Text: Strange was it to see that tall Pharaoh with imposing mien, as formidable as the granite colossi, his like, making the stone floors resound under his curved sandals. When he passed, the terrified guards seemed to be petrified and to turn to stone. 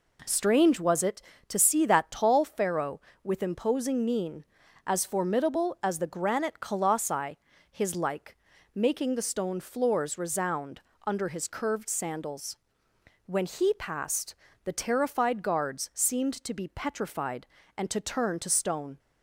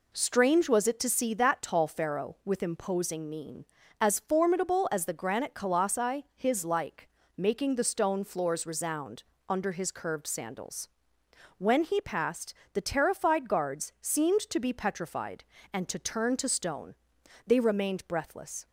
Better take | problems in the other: first | pauses between "resound" and "under"; slight; at 9.2 s; 0.26 s long; slight in the first // goes on to say "They remained breathless"; noticeable; from 17.4 s on; 1.2 s long

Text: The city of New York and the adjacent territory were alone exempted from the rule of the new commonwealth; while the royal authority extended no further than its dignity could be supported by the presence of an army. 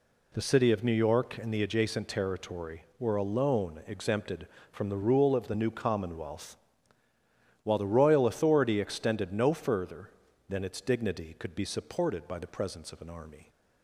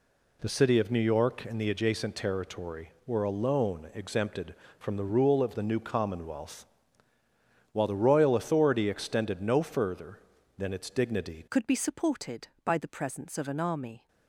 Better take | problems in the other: first | changes voice at "could"; from 11.4 s on; 2.6 s long

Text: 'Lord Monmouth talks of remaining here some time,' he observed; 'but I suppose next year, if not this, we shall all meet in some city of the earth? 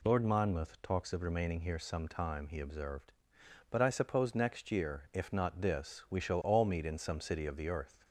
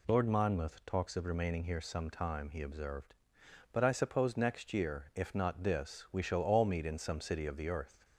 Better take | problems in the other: neither | none

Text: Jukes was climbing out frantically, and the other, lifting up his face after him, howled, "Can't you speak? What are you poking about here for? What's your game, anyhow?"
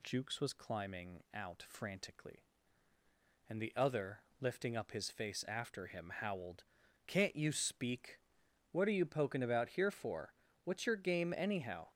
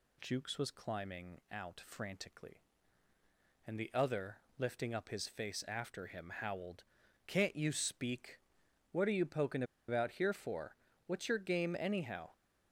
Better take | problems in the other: first | pauses between "poking" and "about"; slight; at 9.6 s; 0.25 s long

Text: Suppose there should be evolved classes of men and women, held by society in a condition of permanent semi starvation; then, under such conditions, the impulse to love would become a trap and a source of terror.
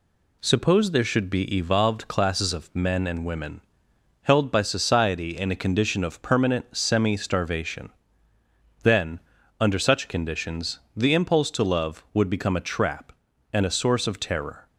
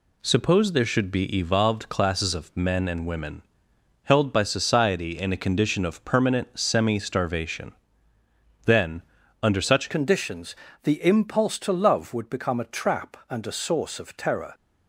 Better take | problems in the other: first | changes voice at "conditions"; from 9.9 s on; 4.6 s long

